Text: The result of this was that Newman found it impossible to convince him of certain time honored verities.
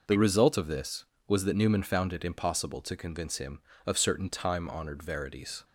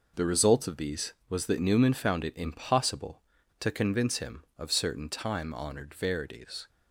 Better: first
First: none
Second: says "these" for "this"; at 0.7 s

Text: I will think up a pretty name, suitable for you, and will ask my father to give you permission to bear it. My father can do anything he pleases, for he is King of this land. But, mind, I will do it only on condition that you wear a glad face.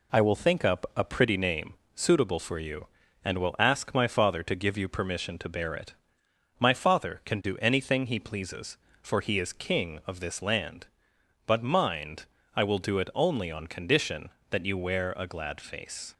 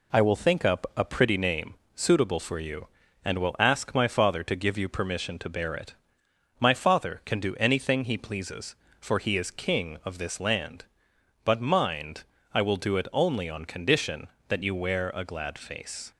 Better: neither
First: none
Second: none

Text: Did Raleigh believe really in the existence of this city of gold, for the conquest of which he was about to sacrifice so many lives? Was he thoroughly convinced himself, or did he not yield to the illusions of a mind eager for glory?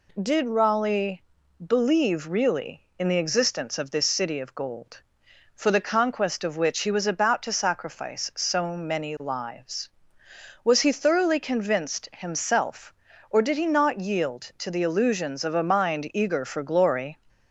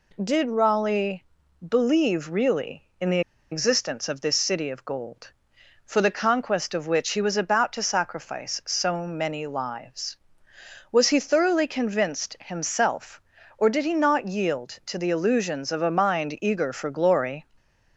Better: first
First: pauses between "Raleigh" and "believe"; at 1.2 s; 0.42 s long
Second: pauses between "Raleigh" and "believe"; at 1.2 s; 0.42 s long // pauses between "the" and "existence"; slight; at 3.2 s; 0.31 s long

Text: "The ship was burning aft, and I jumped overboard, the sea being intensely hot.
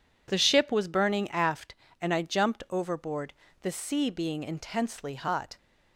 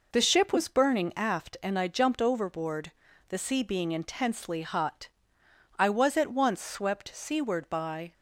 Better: first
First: none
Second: goes on to say "I was at once swept seaward by"; strong; from 5.7 s on; 2.3 s long

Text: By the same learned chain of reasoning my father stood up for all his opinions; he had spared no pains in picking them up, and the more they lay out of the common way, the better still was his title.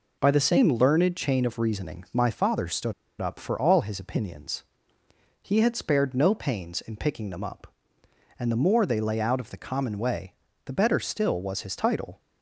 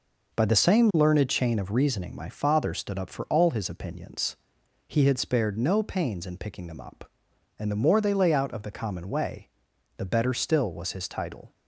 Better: second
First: pauses between "stood" and "up"; slight; at 2.9 s; 0.27 s long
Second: none

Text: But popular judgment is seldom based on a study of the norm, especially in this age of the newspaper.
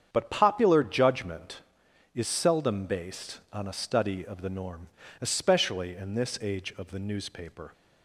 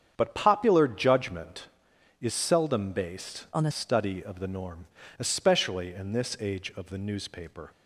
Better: first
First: starts louder than the rest; strong; until 1.1 s; 8 dB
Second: starts louder than the rest; strong; until 1.1 s; 8 dB // changes voice from "on" to "a"; from 3.5 to 3.7 s; 0.2 s long

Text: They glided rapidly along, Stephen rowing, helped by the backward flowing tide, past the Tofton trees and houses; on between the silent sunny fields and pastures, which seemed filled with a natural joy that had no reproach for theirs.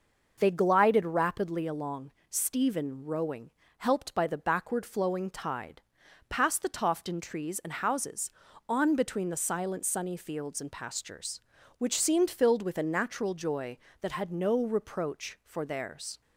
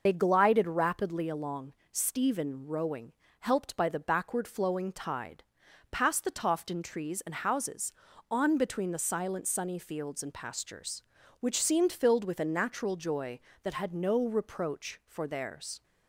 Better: first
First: none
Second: loses the start of "They"; at 0.0 s; 55 ms

